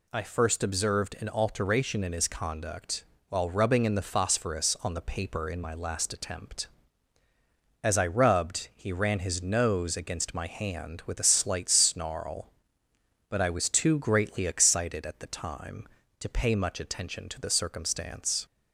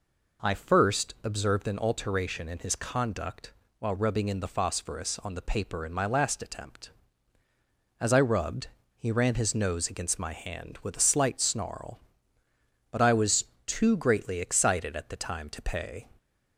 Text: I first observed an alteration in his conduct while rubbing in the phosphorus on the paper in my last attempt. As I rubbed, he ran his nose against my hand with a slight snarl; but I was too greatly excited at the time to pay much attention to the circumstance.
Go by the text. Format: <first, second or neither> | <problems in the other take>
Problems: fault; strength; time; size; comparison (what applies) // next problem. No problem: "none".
first | pauses between "conduct" and "while"; slight; at 3.5 s; 0.26 s long; slight in the first // pauses between "was" and "too"; slight; at 13.4 s; 0.20 s long // stops before "much attention to the circumstance"; at 16.1 s